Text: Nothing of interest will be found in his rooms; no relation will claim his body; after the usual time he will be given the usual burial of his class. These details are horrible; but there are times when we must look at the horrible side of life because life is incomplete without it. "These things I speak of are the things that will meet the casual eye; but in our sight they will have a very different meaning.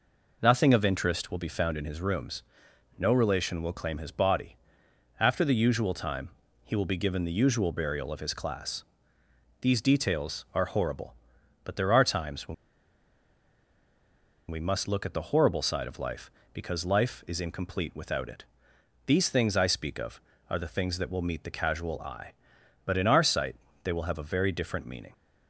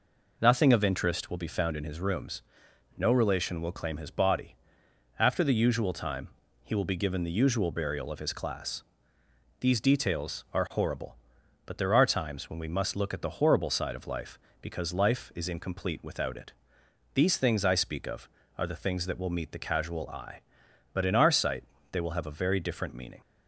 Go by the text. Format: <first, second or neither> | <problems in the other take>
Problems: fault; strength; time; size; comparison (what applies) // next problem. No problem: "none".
second | pauses between "time" and "he"; slight; at 6.2 s; 0.34 s long; slight in the second // pauses between "when" and "we"; strong; at 12.5 s; 1.9 s long // pauses between "sight" and "they"; slight; at 23.5 s; 0.26 s long; slight in the second